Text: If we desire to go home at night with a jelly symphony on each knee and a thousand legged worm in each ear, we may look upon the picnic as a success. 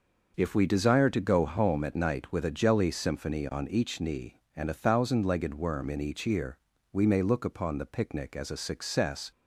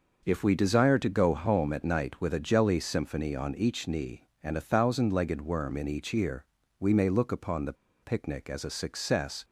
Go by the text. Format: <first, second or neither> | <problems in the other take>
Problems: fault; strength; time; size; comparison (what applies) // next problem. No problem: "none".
first | starts louder than the rest; noticeable; until 1.2 s; 6 dB; also in the first // pauses between "the" and "picnic"; slight; at 7.7 s; 0.28 s long